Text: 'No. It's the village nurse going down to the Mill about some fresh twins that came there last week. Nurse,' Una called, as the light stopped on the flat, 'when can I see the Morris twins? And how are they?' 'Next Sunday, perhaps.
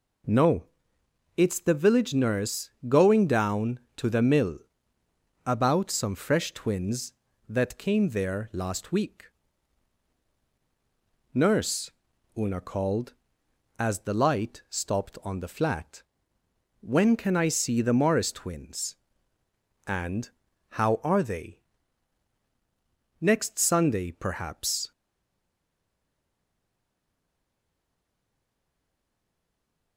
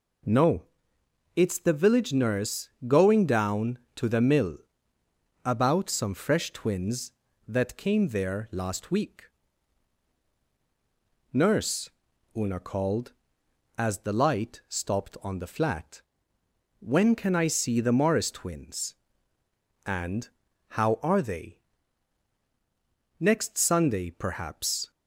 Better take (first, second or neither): second